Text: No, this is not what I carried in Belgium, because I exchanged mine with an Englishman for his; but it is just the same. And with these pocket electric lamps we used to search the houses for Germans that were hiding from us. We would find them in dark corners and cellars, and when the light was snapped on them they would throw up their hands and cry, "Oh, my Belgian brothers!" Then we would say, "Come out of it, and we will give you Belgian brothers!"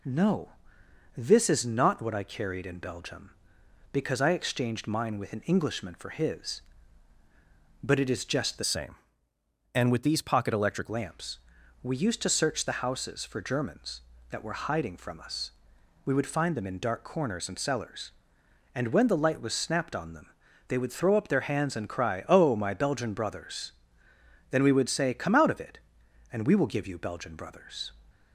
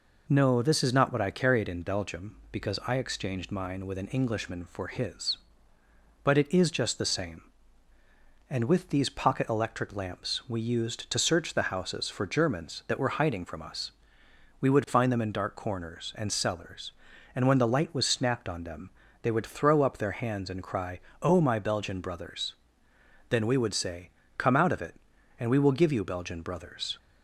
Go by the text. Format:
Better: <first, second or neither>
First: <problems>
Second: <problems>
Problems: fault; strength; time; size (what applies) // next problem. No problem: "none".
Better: second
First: changes voice from "same" to "electric"; from 8.6 to 10.8 s; 2.2 s long // pauses between "lamps" and "we"; at 11.3 s; 0.44 s long // pauses between "them" and "they"; at 20.2 s; 0.42 s long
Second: pauses between "them" and "they"; slight; at 18.8 s; 0.32 s long